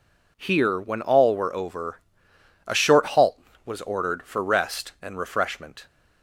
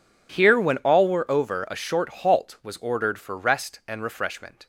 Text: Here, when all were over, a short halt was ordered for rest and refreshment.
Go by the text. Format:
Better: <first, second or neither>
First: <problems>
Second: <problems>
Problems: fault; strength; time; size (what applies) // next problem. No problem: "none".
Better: neither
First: none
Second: none